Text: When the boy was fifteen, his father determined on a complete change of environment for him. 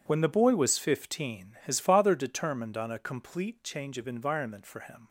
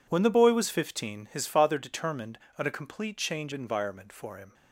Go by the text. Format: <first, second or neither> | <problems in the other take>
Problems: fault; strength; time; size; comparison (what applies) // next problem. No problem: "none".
first | skips "of"; at 3.5 s